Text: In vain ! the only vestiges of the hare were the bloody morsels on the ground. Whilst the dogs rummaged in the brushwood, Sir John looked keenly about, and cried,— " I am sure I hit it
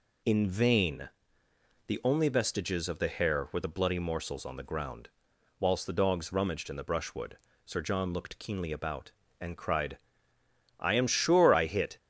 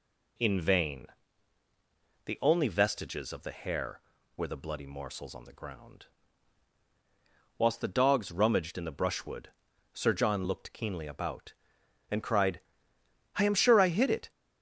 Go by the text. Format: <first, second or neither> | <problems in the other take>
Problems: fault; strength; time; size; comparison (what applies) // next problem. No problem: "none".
second | stops before "it"; at 11.9 s